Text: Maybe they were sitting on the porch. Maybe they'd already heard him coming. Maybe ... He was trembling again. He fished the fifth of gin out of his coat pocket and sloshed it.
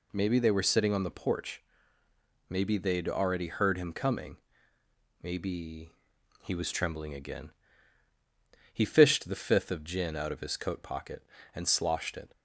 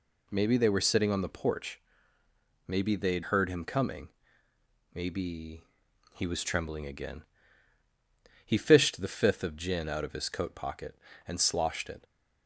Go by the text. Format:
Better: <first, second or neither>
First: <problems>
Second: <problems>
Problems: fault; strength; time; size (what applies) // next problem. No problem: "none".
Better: first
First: none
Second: skips "already"; at 3.2 s